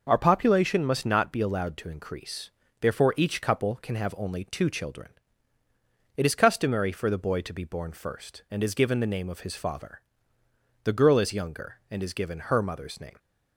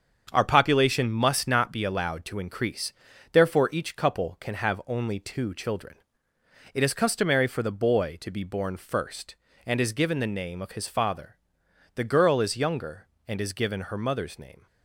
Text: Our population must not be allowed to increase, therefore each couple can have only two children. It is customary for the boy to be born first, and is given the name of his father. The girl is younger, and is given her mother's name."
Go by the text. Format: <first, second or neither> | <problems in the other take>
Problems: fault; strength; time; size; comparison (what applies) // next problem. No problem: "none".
first | gets quieter; strong; throughout; 7 dB